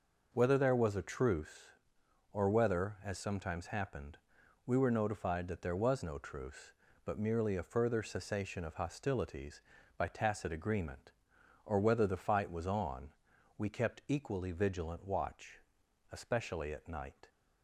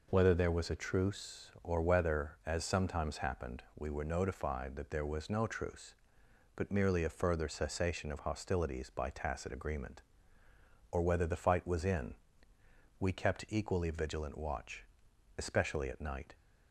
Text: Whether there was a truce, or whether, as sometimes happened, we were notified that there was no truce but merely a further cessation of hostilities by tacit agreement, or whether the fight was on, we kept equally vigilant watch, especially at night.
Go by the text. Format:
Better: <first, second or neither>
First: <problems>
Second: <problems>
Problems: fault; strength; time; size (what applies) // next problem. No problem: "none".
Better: first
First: none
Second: says "in" for "on"; at 11.8 s